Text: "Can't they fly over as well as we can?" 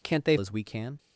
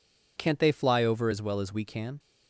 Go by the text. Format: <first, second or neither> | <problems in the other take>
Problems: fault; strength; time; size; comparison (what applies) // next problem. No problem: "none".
second | skips "fly over as well"; at 0.3 s